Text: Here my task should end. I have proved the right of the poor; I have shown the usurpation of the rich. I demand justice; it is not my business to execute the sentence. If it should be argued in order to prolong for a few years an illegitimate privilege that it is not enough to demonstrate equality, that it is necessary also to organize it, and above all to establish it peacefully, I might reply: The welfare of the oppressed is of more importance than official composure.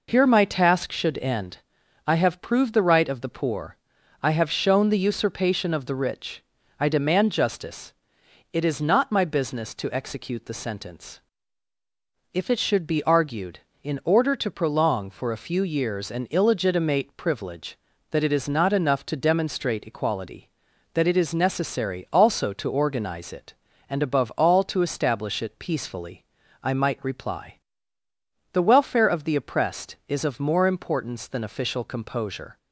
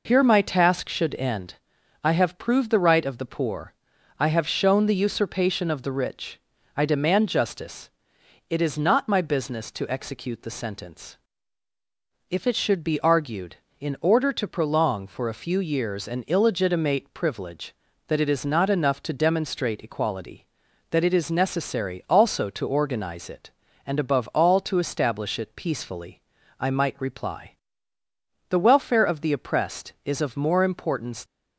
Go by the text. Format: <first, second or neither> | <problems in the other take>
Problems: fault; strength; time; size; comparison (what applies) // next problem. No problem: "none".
first | stops before "than official composure"; at 31.2 s